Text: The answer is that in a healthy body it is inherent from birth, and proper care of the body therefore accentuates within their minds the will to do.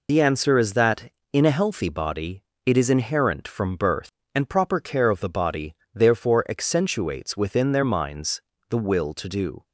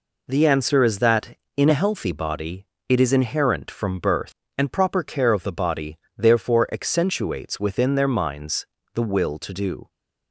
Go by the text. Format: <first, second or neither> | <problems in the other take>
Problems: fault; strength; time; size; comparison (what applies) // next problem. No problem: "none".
second | loses the start of "The"; at 0.0 s; 65 ms // pauses between "body" and "it"; slight; at 2.4 s; 0.22 s long; slight in the second // pauses between "body" and "therefore"; slight; at 5.7 s; 0.20 s long; slight in the second // pauses between "minds" and "the"; slight; at 8.4 s; 0.28 s long; slight in the second